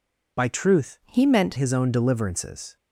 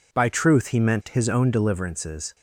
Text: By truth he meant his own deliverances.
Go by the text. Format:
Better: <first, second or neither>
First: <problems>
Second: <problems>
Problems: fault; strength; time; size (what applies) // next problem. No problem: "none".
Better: second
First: changes voice from "he" to "meant"; from 1.0 to 1.5 s; 0.5 s long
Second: none